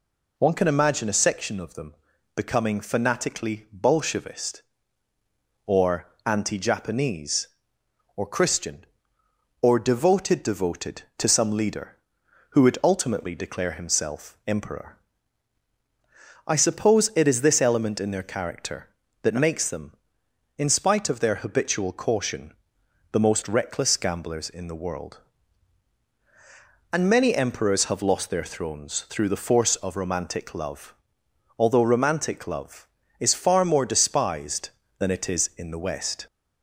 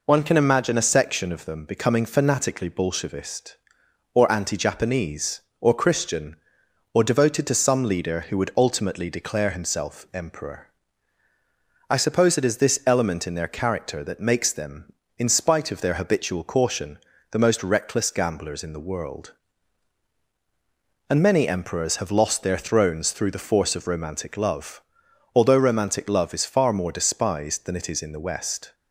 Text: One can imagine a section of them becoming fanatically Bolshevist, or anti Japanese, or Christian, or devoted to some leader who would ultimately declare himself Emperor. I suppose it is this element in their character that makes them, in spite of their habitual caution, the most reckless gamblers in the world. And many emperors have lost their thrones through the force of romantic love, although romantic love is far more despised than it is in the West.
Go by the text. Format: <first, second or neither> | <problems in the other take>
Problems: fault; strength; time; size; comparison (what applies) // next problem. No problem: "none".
second | pauses between "them" and "becoming"; at 1.9 s; 0.40 s long // pauses between "or" and "anti"; slight; at 6.0 s; 0.18 s long // says "devoted" twice; at 10.4 s